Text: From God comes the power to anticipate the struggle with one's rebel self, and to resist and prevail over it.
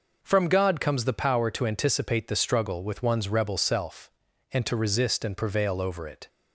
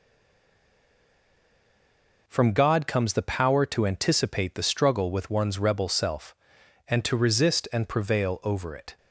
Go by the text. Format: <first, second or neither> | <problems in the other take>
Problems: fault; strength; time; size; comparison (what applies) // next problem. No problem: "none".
first | stays silent before the first word; until 2.2 s; 2.2 s long